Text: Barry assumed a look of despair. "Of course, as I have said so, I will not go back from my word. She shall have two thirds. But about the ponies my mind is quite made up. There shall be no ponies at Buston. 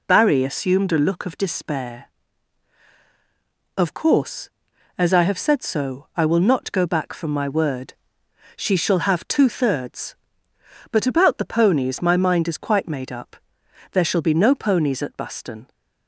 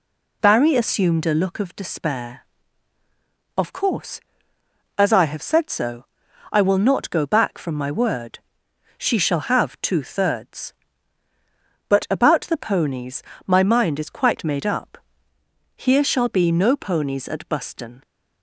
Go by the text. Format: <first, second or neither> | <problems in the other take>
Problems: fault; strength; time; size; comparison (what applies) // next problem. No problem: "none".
first | pauses between "ponies" and "my"; slight; at 13.2 s; 0.24 s long // says "Here" for "There"; at 15.7 s